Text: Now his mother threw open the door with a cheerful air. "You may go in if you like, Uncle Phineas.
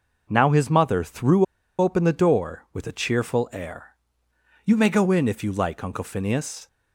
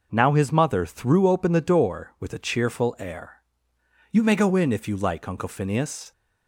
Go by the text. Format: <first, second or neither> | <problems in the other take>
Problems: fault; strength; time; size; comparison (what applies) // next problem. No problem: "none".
second | pauses between "threw" and "open"; slight; at 1.4 s; 0.34 s long